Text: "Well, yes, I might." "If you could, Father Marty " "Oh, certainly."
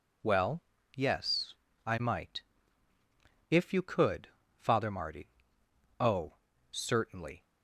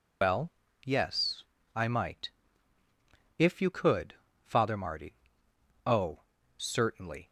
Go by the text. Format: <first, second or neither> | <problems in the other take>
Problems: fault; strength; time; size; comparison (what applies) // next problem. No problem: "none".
first | loses the start of "Well"; at 0.2 s; 100 ms